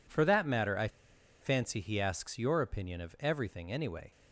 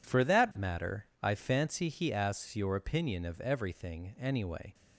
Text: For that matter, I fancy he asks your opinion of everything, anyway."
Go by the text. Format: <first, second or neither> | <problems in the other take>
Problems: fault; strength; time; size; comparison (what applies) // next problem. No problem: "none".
second | pauses between "I" and "fancy"; noticeable; at 0.8 s; 0.53 s long